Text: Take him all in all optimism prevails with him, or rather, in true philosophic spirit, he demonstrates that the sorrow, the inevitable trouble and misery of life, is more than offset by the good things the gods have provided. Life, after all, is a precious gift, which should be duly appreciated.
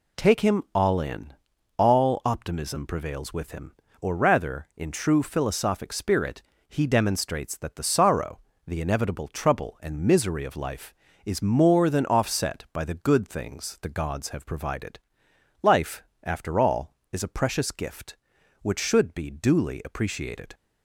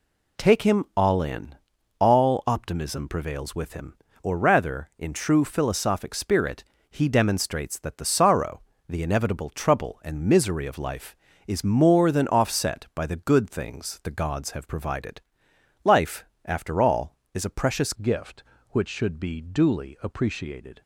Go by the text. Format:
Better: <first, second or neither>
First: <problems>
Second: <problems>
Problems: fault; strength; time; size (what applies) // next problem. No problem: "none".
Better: first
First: pauses between "in" and "all"; at 1.3 s; 0.42 s long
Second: pauses between "in" and "all"; at 1.5 s; 0.42 s long // changes voice at "gift"; from 17.9 s on; 2.9 s long